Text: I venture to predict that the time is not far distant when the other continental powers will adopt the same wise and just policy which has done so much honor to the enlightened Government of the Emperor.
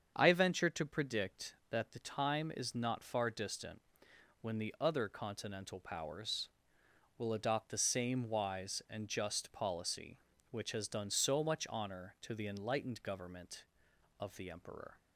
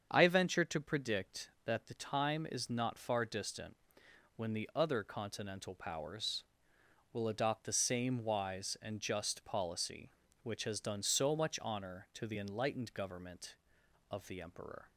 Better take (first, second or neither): neither